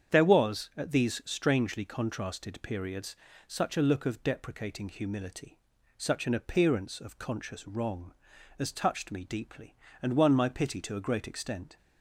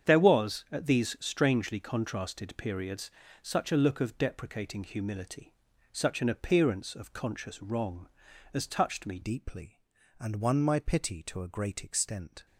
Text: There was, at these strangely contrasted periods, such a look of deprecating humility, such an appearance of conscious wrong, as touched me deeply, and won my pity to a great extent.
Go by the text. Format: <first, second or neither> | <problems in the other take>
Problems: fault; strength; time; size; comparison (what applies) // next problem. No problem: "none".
first | starts louder than the rest; strong; until 1.1 s; 8 dB; strong in the first // changes voice at "deeply"; from 9.2 s on; 3.2 s long